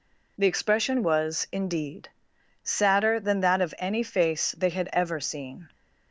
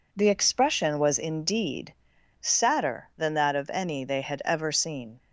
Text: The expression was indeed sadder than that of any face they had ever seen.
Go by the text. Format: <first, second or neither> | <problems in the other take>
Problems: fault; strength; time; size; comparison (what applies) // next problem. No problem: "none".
first | pauses between "indeed" and "sadder"; noticeable; at 1.9 s; 0.46 s long; noticeable in the first // skips "face"; at 4.0 s